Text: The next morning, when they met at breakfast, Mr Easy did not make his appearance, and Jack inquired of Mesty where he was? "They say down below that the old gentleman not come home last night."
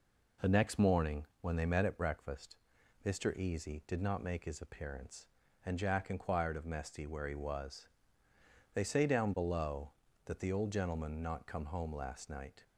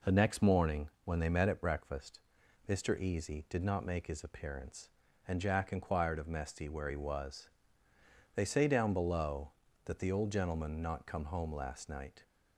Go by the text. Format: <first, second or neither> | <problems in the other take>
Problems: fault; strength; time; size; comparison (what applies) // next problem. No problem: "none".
neither | none